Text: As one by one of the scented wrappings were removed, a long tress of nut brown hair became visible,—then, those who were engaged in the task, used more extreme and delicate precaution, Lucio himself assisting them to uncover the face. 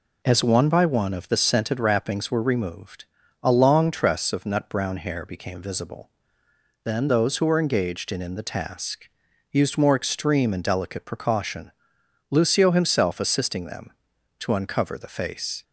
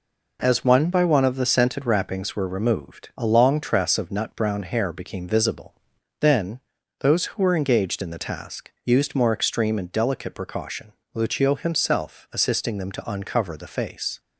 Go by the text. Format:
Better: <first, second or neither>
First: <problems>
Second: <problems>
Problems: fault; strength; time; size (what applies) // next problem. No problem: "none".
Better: second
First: says "in" twice; at 8.2 s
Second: none